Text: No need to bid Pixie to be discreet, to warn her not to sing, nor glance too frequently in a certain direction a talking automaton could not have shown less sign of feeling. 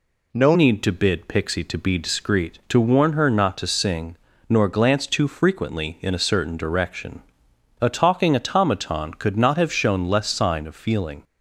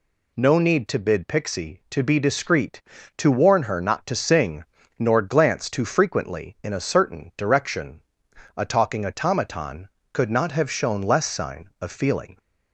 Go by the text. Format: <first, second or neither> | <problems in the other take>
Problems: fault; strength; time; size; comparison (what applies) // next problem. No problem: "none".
second | changes voice at "need"; from 0.5 s on; 10.7 s long // pauses between "direction" and "a"; noticeable; at 7.2 s; 0.60 s long; noticeable in the second